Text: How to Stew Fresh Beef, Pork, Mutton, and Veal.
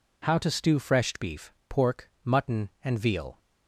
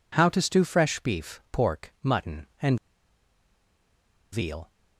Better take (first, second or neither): first